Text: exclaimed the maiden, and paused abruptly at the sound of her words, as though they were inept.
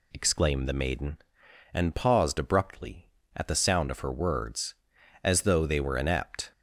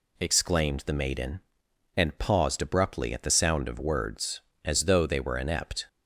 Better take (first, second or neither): first